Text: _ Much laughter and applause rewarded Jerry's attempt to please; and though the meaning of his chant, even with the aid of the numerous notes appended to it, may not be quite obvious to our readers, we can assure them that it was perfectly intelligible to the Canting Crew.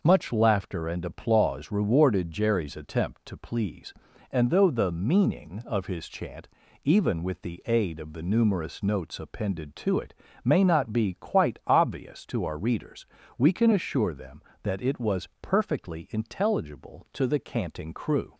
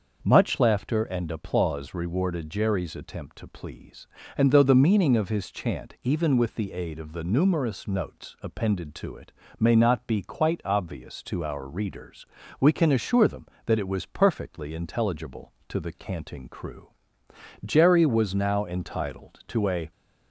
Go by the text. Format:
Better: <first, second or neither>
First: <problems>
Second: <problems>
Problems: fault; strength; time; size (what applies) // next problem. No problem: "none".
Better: first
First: none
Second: starts louder than the rest; until 1.2 s; 6 dB // goes on to say "Jerry was now entitled to a"; strong; from 17.6 s on; 2.2 s long